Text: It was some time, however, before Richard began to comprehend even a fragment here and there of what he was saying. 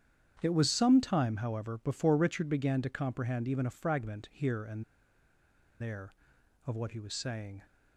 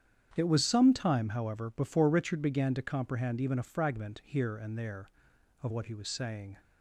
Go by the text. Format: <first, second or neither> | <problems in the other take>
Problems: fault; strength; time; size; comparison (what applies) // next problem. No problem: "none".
second | starts louder than the rest; strong; until 1.4 s; 9 dB; strong in the second // pauses between "and" and "there"; at 4.8 s; 0.98 s long